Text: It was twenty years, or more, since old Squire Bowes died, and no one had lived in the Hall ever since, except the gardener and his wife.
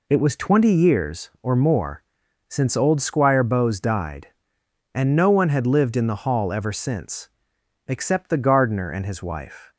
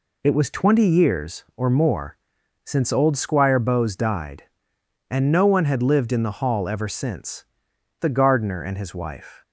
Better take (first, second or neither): first